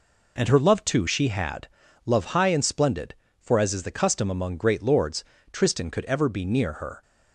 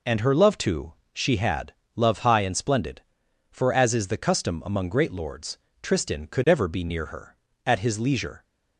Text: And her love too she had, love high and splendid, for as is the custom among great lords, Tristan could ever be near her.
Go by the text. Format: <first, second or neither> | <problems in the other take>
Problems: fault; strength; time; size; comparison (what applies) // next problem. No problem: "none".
first | pauses between "too" and "she"; slight; at 0.9 s; 0.20 s long // goes on to say "At his leisure"; noticeable; from 7.6 s on; 0.78 s long